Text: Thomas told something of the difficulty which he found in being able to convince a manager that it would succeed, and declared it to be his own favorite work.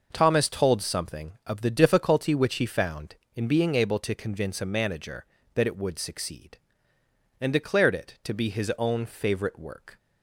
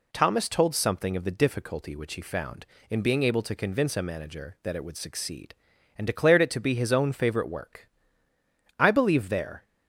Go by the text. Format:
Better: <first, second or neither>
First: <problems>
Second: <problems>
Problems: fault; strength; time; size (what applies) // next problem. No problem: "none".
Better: first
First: none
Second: goes on to say "I believe there"; noticeable; from 8.7 s on; 0.86 s long